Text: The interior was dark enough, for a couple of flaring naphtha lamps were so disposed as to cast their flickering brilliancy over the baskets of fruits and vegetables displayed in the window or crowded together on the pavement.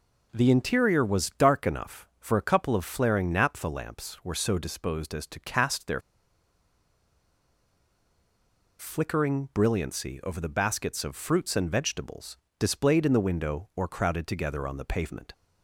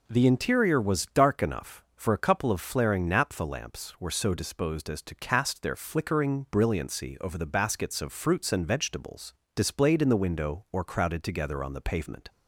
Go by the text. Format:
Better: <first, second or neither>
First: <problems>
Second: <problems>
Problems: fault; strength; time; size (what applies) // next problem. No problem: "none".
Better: second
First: pauses between "their" and "flickering"; strong; at 5.9 s; 2.7 s long // pauses between "vegetables" and "displayed"; slight; at 12.3 s; 0.24 s long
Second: pauses between "vegetables" and "displayed"; slight; at 9.3 s; 0.24 s long